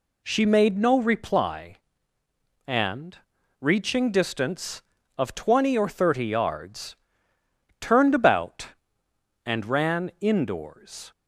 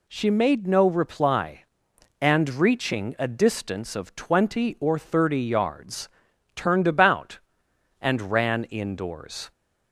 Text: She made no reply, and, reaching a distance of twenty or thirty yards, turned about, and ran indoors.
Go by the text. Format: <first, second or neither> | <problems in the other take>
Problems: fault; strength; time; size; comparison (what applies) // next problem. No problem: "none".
second | skips "a"; at 4.0 s